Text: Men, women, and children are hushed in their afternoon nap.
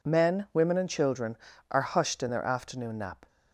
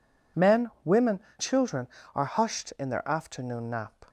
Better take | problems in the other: first | skips "and"; at 1.2 s

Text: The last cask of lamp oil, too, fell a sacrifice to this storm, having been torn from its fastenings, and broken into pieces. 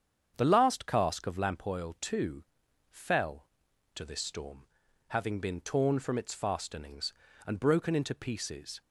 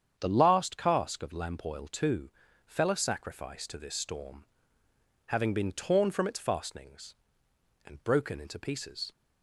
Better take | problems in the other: second | starts louder than the rest; strong; until 1.3 s; 8 dB; strong in the second // skips "a sacrifice"; at 3.7 s

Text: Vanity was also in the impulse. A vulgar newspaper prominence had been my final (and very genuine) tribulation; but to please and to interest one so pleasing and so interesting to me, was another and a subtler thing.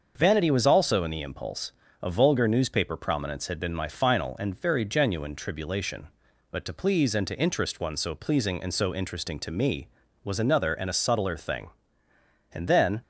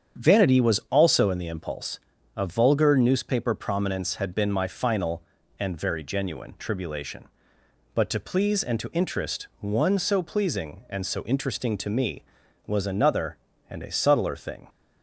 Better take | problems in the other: second | starts louder than the rest; until 1.1 s; 6.5 dB; strong in the second // goes on to say "And then"; from 12.5 s on; 0.52 s long

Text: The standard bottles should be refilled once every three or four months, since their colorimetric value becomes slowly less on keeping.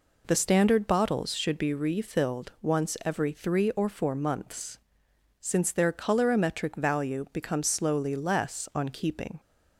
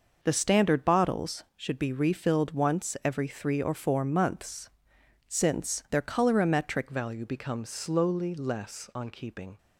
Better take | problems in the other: first | changes voice at "value"; from 6.8 s on; 2.7 s long

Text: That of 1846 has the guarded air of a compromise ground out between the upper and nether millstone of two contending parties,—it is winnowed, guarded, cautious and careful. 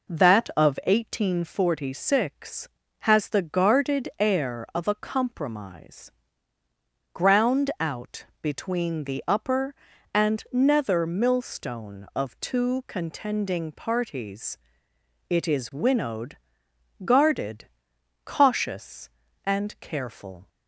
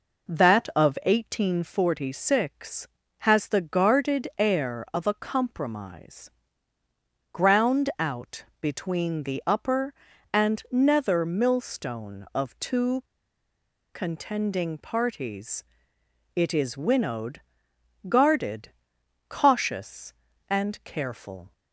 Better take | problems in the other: first | pauses between "compromise" and "ground"; at 6.2 s; 1.0 s long; also in the first // pauses between "out" and "between"; slight; at 8.4 s; 0.16 s long; slight in the first // pauses between "two" and "contending"; noticeable; at 13.0 s; 0.90 s long

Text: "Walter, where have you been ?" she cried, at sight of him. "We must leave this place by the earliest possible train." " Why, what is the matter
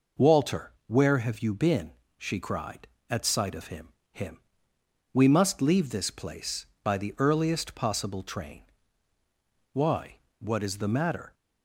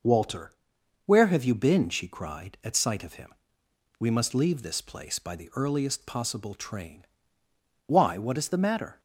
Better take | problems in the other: second | says "him" twice; at 4.1 s

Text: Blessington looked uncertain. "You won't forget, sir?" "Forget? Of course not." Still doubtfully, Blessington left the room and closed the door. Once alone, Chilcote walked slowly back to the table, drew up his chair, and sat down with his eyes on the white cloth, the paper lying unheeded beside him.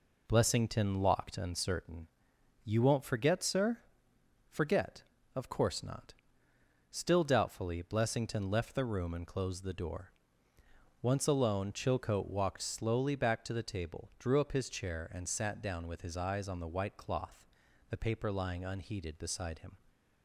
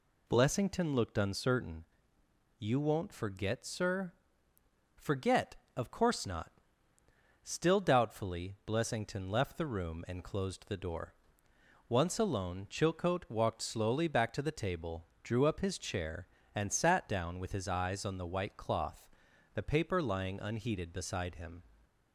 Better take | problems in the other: second | says "locked" for "looked"; at 1.0 s

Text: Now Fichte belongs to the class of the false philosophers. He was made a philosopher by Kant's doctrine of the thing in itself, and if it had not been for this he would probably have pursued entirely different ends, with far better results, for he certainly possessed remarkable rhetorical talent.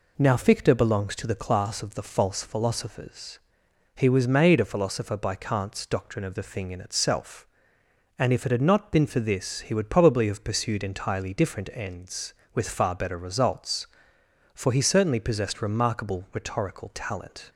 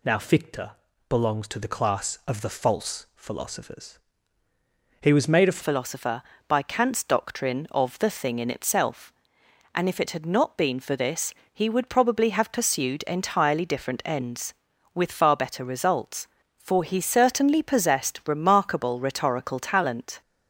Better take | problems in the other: first | pauses between "Fichte" and "belongs"; at 0.7 s; 0.40 s long // changes voice at "philosopher"; from 5.6 s on; 14.6 s long // pauses between "this" and "he"; slight; at 11.3 s; 0.20 s long

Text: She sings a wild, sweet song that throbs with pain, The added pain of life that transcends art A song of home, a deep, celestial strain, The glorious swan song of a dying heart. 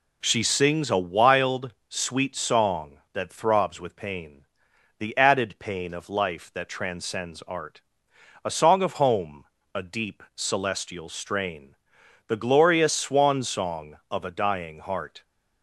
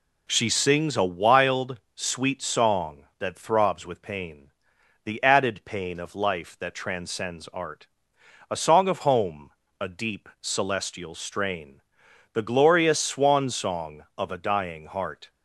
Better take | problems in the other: neither | pauses between "art" and "A"; noticeable; the same in both

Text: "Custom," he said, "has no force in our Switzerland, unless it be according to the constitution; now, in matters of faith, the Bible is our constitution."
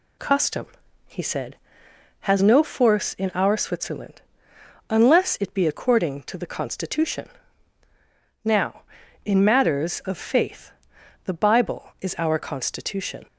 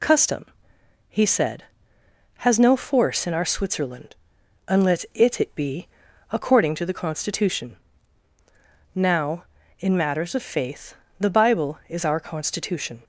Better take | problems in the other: first | says "it" twice; at 5.3 s // pauses between "be" and "according"; noticeable; at 5.8 s; 0.46 s long

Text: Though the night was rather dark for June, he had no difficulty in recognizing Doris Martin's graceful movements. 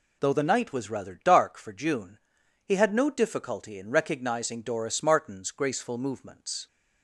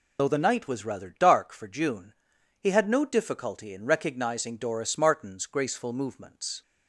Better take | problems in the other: first | loses the start of "Though"; at 0.1 s; 40 ms

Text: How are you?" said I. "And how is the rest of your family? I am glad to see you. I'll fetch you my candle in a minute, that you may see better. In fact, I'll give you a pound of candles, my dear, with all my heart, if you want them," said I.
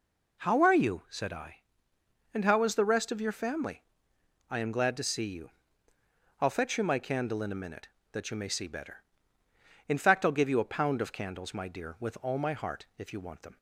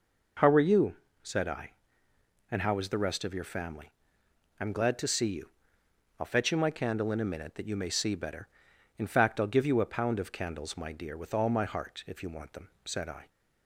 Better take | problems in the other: second | stops before "said I"; at 13.5 s

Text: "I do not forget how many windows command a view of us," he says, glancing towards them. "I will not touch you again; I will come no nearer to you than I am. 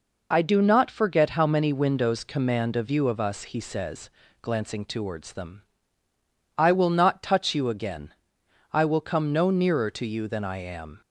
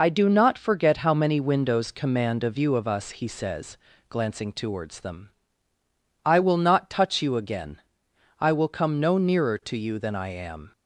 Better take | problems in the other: first | loses the start of "I"; at 0.0 s; 20 ms

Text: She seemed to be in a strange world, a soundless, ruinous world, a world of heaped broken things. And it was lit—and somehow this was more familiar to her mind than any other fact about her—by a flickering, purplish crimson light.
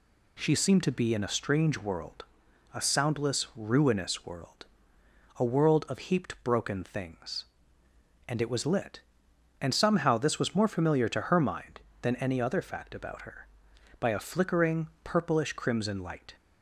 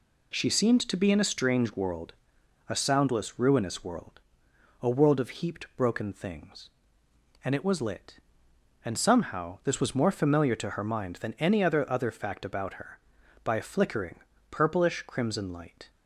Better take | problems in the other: first | says "other" twice; at 11.8 s

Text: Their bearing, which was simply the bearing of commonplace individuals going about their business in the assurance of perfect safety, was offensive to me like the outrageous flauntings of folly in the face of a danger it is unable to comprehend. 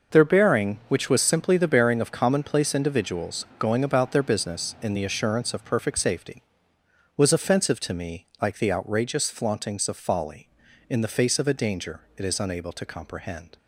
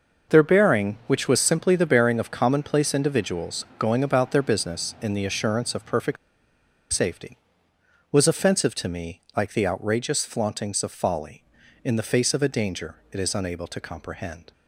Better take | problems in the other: first | pauses between "perfect" and "safety"; noticeable; at 6.1 s; 0.75 s long // pauses between "danger" and "it"; slight; at 12.9 s; 0.16 s long; slight in the first

